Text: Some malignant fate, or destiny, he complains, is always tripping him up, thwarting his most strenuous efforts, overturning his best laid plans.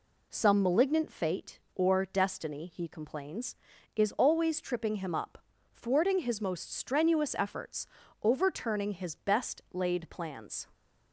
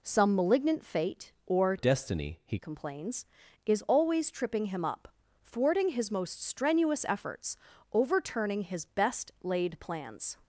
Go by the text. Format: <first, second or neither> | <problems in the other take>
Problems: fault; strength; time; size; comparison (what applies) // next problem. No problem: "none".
first | changes voice from "destiny" to "he"; from 1.7 to 2.5 s; 0.8 s long